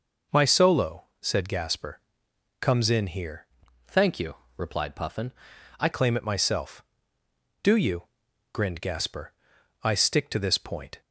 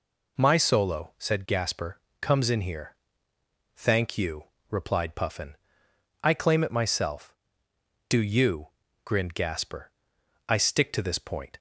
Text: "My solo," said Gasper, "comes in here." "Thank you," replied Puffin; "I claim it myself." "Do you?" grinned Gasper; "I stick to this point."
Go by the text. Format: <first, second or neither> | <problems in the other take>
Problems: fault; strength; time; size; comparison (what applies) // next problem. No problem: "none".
second | changes voice from "Thank" to "I"; from 3.8 to 5.8 s; 2.0 s long